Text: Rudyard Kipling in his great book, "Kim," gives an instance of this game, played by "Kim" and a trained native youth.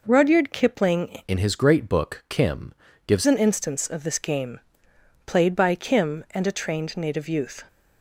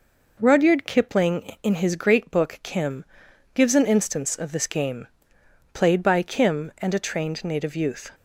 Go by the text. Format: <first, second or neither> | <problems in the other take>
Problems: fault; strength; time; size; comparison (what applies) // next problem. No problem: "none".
second | changes voice from "in" to "gives"; from 1.2 to 3.2 s; 2.0 s long